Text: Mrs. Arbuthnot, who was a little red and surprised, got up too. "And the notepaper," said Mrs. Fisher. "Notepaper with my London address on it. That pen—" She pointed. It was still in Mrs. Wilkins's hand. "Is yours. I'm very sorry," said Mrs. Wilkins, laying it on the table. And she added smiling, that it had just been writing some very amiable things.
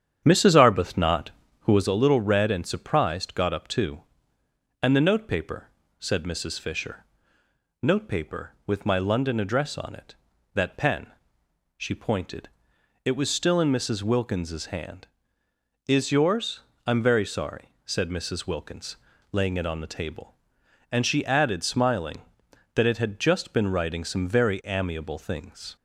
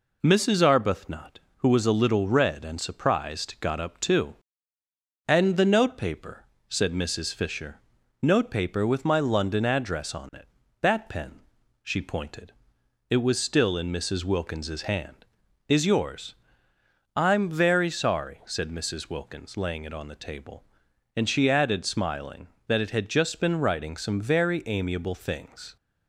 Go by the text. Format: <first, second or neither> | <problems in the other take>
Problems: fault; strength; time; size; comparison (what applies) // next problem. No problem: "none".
second | starts louder than the rest; strong; until 1.9 s; 8.5 dB